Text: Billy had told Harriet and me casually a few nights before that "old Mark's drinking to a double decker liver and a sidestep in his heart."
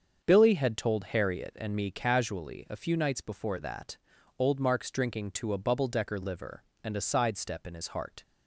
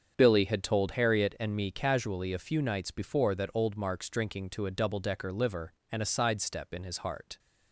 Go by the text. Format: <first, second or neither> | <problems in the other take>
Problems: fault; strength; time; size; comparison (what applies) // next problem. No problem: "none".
second | starts louder than the rest; until 1.2 s; 6.5 dB; strong in the second // pauses between "that" and "old"; at 3.9 s; 0.42 s long // says "bubble" for "double"; at 5.5 s